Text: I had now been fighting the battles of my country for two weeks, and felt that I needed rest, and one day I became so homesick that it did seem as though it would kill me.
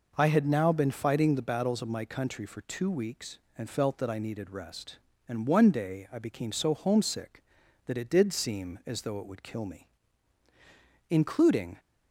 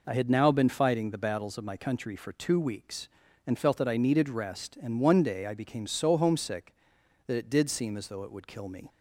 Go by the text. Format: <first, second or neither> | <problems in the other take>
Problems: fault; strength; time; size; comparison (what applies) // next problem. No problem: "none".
second | goes on to say "Including"; noticeable; from 11.1 s on; 0.68 s long